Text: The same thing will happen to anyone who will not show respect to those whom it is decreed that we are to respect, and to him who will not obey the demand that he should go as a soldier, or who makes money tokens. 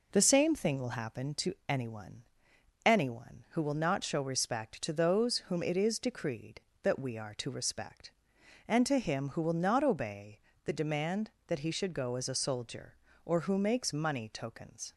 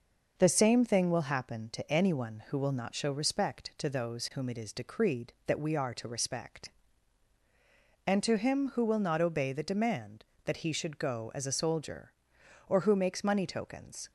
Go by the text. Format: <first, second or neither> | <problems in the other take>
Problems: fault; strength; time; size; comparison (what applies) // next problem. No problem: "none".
second | says "anyone" twice; at 2.8 s // pauses between "obey" and "the"; slight; at 10.3 s; 0.24 s long